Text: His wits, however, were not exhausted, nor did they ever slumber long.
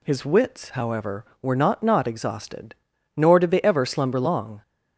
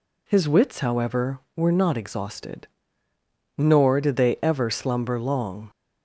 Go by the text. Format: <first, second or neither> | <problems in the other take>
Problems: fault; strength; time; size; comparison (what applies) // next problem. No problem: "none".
second | says "not" twice; at 1.8 s